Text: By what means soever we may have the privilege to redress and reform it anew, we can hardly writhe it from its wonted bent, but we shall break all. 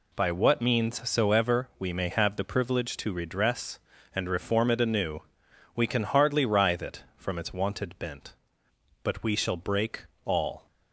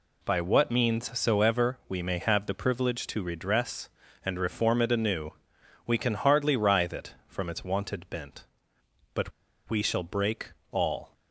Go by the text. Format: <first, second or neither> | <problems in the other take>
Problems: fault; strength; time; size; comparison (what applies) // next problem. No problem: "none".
first | pauses between "but" and "we"; at 9.3 s; 0.38 s long // pauses between "break" and "all"; slight; at 10.5 s; 0.18 s long; slight in the first